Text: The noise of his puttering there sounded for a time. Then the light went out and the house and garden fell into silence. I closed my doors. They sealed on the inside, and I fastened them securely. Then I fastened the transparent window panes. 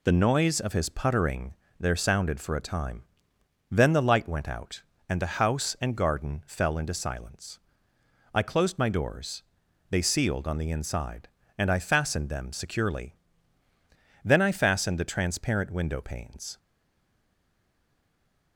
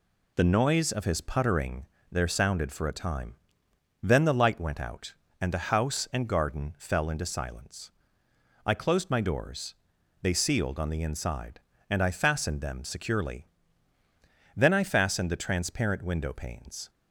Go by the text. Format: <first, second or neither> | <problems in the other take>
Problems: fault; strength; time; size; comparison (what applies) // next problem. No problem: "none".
second | pauses between "puttering" and "there"; slight; at 1.5 s; 0.26 s long; slight in the second // stays silent after the last word; noticeable; from 16.5 s on; 2.0 s long